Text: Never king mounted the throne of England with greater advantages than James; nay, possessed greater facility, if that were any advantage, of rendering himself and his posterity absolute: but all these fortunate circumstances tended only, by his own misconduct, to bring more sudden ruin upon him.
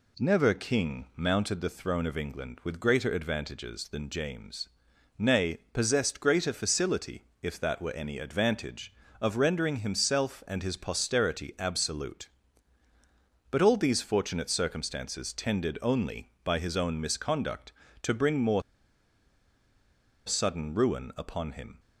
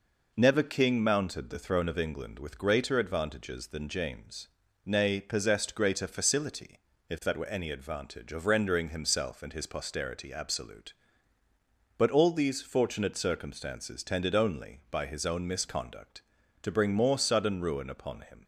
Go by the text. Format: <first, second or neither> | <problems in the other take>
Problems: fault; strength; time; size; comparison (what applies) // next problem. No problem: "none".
second | pauses between "more" and "sudden"; strong; at 18.6 s; 1.6 s long